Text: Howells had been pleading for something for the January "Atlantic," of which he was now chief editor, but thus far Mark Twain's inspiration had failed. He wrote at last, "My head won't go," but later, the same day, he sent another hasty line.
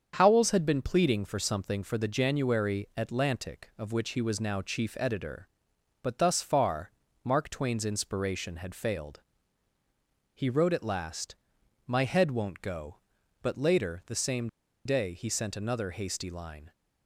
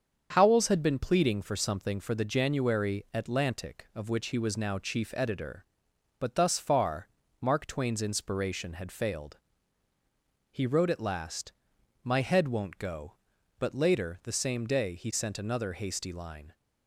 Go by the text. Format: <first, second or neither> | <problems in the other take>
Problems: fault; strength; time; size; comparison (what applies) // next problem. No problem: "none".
second | starts louder than the rest; strong; until 1.1 s; 7.5 dB; strong in the second // pauses between "far" and "Mark"; slight; at 6.9 s; 0.32 s long; slight in the second // pauses between "same" and "day"; at 14.4 s; 0.37 s long